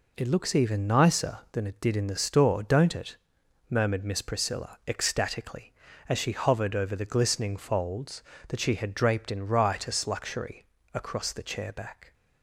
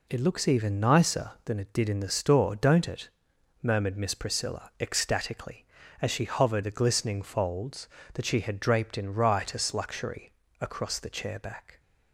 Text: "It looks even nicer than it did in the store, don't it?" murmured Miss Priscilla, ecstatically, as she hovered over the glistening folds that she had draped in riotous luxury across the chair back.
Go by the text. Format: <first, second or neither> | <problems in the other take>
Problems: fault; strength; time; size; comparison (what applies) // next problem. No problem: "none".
first | skips "over"; at 6.6 s // pauses between "luxury" and "across"; slight; at 10.3 s; 0.28 s long; slight in the first